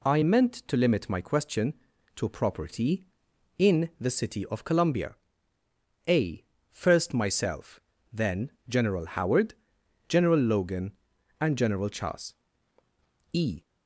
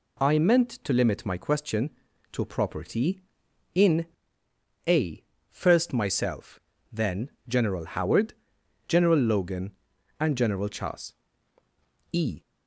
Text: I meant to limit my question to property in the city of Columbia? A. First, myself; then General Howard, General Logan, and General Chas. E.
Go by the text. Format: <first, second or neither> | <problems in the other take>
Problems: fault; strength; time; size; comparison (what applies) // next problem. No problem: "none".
first | skips "the city of Columbia"; at 4.4 s // pauses between "then" and "General"; slight; at 7.2 s; 0.18 s long; slight in the first